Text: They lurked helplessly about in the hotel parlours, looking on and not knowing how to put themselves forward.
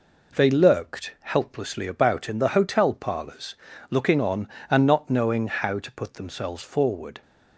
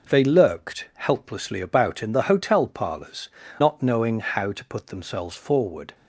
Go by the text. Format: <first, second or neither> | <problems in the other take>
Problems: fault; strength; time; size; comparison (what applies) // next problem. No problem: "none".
first | skips "looking on and"; at 3.4 s